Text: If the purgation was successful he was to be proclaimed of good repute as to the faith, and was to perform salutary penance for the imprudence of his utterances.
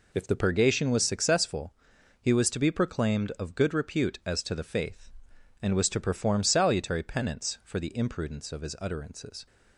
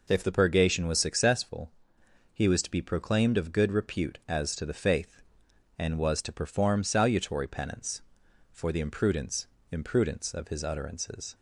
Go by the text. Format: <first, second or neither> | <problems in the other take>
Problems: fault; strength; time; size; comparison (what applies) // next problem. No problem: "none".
first | pauses between "successful" and "he"; noticeable; at 1.7 s; 0.62 s long; noticeable in the first // says "imprudence" twice; at 9.7 s